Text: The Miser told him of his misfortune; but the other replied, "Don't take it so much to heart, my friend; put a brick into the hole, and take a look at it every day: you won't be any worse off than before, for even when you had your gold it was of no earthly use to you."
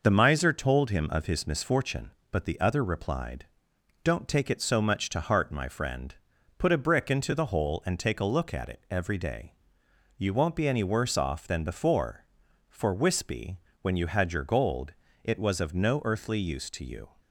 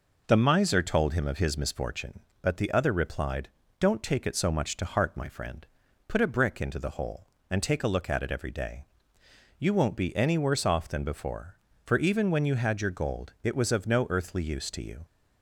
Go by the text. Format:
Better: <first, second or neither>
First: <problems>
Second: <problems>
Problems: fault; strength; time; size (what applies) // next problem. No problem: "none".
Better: second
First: says "wispy" for "even"; at 12.9 s // pauses between "gold" and "it"; slight; at 14.9 s; 0.32 s long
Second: none